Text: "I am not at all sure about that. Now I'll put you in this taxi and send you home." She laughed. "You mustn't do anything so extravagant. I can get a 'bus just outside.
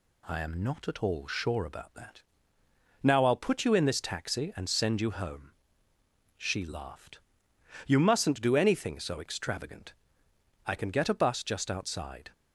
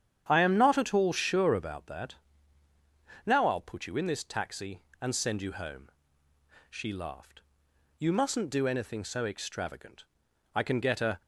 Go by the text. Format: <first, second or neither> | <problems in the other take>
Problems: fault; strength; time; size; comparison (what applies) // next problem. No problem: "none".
first | starts louder than the rest; strong; until 1.2 s; 9 dB // stops before "bus just outside"; at 11.2 s